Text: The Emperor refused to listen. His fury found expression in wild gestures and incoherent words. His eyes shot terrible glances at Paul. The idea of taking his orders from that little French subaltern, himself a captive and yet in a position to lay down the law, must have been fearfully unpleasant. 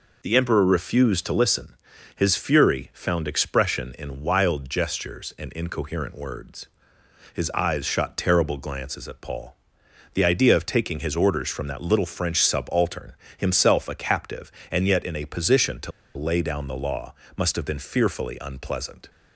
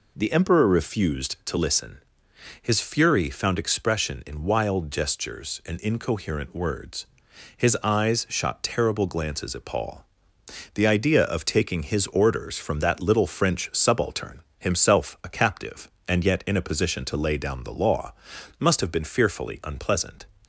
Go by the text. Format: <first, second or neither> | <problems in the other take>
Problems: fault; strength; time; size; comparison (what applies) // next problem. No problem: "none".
second | pauses between "to" and "lay"; slight; at 15.9 s; 0.24 s long